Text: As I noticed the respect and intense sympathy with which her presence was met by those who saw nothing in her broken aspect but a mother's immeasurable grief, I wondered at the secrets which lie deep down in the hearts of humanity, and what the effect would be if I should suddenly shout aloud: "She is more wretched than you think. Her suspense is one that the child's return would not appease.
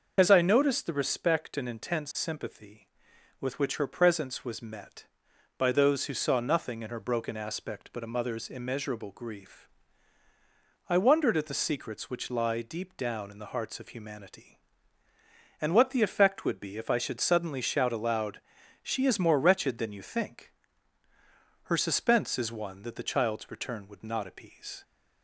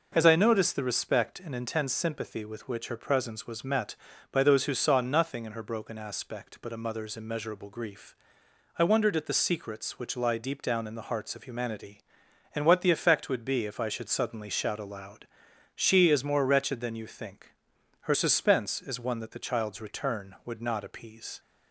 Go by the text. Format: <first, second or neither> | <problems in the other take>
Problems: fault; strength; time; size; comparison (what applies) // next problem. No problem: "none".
second | loses the start of "As"; at 0.1 s; 35 ms // starts louder than the rest; until 1.1 s; 6.5 dB